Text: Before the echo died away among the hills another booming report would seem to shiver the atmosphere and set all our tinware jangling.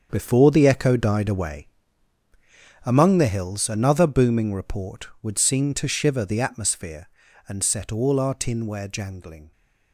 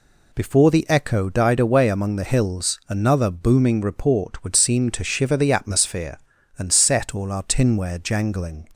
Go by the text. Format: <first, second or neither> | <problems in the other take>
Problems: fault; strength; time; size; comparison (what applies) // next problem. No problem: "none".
second | gets quieter; strong; throughout; 12 dB // pauses between "away" and "among"; at 1.6 s; 1.1 s long